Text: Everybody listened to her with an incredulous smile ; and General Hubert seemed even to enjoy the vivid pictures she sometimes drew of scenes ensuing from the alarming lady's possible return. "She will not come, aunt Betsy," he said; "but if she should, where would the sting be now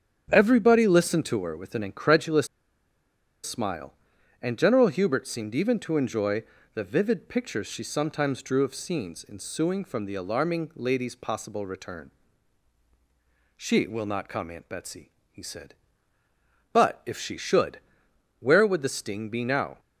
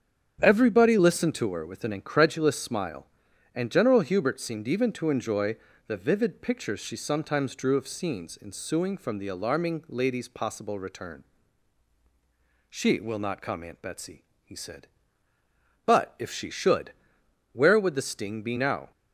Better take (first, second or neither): second